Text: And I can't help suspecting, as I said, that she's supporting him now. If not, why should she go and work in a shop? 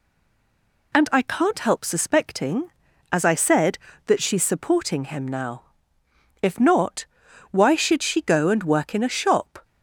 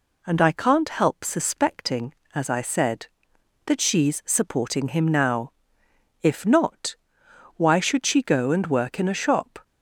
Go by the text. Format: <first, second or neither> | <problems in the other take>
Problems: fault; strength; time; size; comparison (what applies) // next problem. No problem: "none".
second | stays silent before the first word; slight; until 0.9 s; 0.9 s long